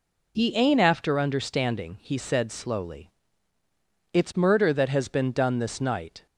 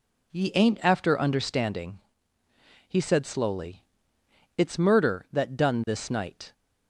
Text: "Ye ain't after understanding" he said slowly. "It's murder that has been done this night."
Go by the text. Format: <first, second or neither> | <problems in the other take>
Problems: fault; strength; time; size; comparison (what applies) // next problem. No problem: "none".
first | pauses between "understanding" and "he"; noticeable; at 1.9 s; 0.90 s long // skips "has been"; at 5.5 s